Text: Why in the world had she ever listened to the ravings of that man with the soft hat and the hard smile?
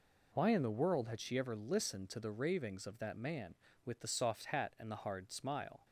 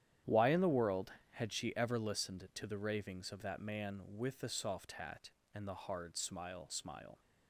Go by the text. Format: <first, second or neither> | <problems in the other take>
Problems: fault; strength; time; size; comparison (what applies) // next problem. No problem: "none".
first | starts louder than the rest; strong; until 1.4 s; 10.5 dB // says "smile" twice; at 6.7 s